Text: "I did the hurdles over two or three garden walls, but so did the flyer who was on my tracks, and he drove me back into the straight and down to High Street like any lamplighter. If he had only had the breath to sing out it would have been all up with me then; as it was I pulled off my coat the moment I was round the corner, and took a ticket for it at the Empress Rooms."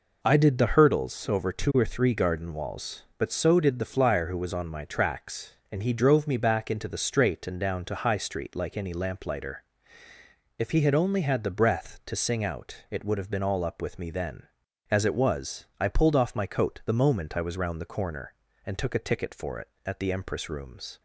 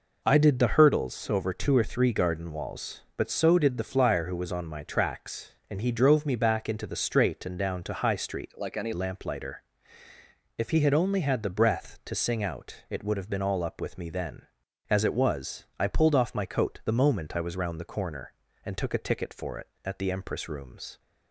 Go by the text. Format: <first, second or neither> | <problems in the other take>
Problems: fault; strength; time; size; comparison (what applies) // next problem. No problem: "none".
first | changes voice from "like" to "any"; from 8.5 to 8.9 s; 0.4 s long